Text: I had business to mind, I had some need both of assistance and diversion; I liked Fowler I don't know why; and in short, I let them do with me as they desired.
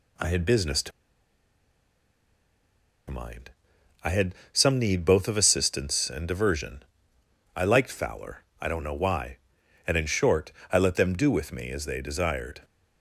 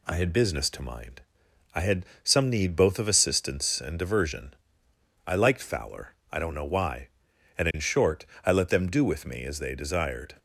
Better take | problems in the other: second | pauses between "to" and "mind"; strong; at 0.9 s; 2.1 s long // pauses between "had" and "some"; slight; at 4.3 s; 0.20 s long; slight in the second // pauses between "Fowler" and "I"; slight; at 8.4 s; 0.16 s long; slight in the second

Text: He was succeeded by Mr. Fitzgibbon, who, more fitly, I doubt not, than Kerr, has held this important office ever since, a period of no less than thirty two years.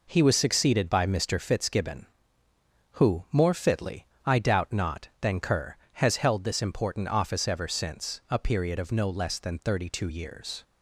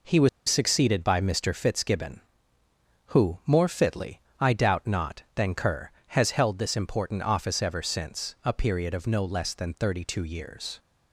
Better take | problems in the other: first | pauses between "was" and "succeeded"; slight; at 0.2 s; 0.19 s long

